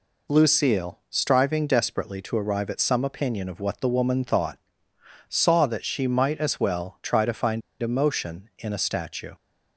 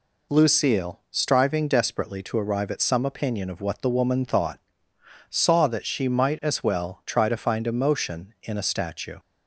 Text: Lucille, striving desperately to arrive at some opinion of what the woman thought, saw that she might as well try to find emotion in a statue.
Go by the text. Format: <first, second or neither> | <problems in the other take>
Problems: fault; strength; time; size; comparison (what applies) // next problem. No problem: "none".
second | pauses between "find" and "emotion"; slight; at 7.6 s; 0.20 s long